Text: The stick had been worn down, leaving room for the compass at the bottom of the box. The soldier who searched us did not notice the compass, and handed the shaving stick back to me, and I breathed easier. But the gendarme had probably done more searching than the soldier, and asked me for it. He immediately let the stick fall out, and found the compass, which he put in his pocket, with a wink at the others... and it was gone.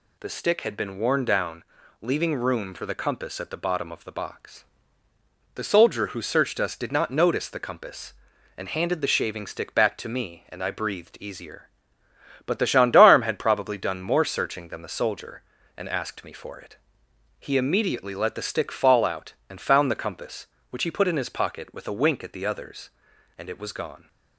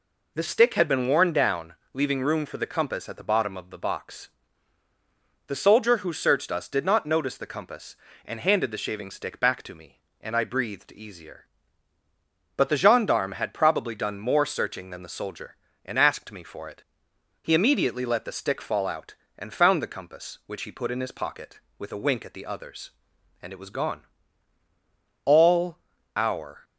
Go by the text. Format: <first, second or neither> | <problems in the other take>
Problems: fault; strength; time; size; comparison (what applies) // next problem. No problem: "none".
first | goes on to say "All our"; from 25.2 s on; 1.3 s long